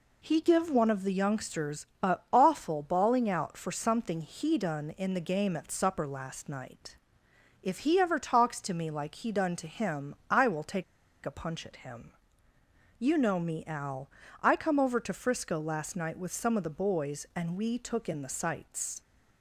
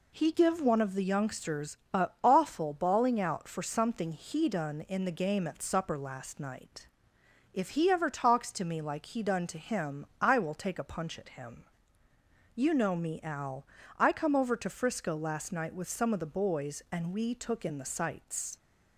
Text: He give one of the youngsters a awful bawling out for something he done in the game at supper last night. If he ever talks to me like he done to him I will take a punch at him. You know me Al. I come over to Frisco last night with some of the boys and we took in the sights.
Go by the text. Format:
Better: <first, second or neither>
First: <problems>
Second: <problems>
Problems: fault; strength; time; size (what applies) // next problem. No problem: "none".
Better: second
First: pauses between "youngsters" and "a"; slight; at 1.8 s; 0.16 s long // pauses between "him" and "I"; slight; at 10.1 s; 0.16 s long // pauses between "take" and "a"; at 10.8 s; 0.40 s long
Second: pauses between "youngsters" and "a"; slight; at 1.7 s; 0.16 s long // pauses between "him" and "I"; slight; at 10.0 s; 0.16 s long